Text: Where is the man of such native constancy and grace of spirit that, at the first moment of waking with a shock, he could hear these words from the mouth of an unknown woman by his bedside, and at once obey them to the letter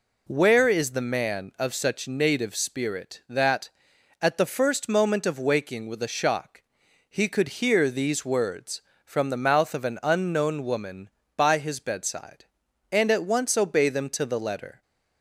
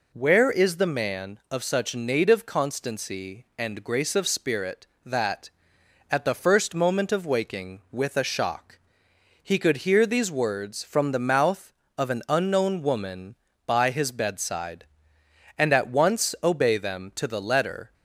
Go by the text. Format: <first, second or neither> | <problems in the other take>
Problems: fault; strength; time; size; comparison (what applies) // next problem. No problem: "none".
second | skips "constancy and grace of"; at 2.5 s